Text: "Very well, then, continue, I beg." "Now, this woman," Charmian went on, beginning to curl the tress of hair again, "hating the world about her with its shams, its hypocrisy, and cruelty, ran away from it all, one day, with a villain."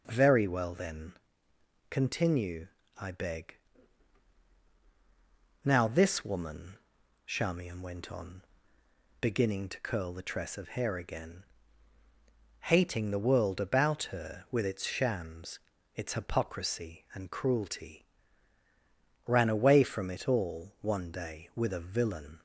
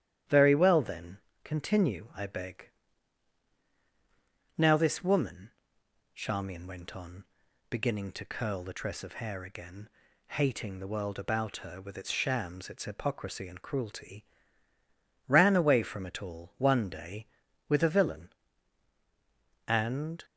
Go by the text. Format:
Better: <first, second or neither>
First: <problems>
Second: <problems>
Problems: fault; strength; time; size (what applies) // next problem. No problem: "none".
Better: first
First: none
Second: starts louder than the rest; strong; until 1.5 s; 11 dB // goes on to say "And"; from 19.6 s on; 0.58 s long